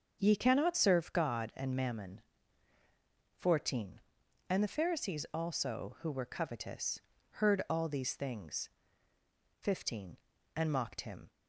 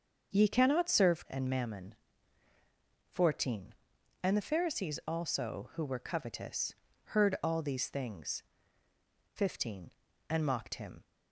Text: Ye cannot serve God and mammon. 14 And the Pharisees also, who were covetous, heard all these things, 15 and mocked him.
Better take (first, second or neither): first